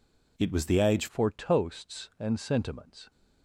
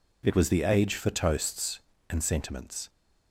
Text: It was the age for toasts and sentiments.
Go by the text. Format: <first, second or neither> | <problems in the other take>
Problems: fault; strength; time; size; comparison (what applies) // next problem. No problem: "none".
second | changes voice at "for"; from 1.0 s on; 2.0 s long